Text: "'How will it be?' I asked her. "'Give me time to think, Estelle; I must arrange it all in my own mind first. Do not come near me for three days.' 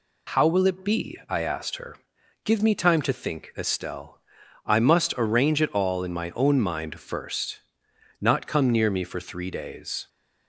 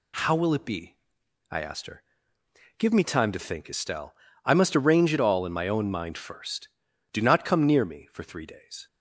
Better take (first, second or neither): second